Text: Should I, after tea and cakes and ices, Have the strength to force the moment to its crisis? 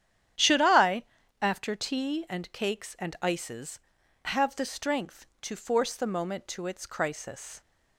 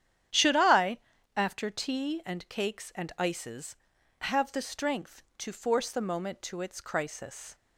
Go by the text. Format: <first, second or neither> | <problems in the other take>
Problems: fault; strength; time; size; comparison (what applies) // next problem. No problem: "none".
neither | starts louder than the rest; strong; the same in both